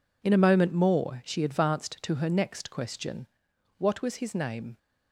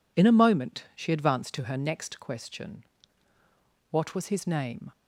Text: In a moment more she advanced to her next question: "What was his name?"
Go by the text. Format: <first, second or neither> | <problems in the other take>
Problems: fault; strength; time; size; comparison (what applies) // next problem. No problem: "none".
first | skips "more"; at 0.9 s